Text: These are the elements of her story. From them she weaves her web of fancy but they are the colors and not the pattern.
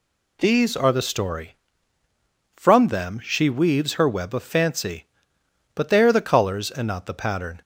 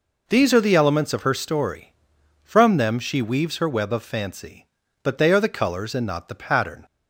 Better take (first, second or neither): second